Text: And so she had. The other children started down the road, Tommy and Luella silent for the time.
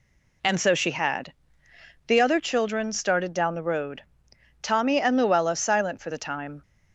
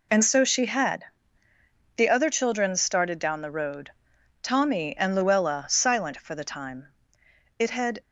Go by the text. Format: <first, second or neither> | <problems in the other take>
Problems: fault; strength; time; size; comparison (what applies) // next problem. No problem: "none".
first | goes on to say "It had"; slight; from 7.5 s on; 0.42 s long